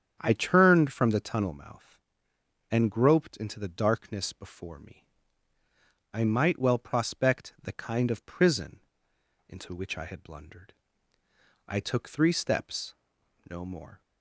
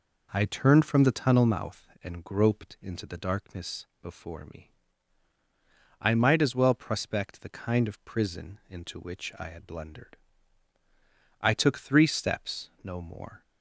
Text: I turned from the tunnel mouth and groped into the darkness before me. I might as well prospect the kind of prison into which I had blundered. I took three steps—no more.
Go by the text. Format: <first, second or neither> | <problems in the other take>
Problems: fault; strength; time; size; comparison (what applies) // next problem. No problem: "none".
second | starts louder than the rest; strong; until 1.2 s; 8.5 dB // skips "as"; at 6.5 s // pauses between "prison" and "into"; noticeable; at 8.8 s; 0.66 s long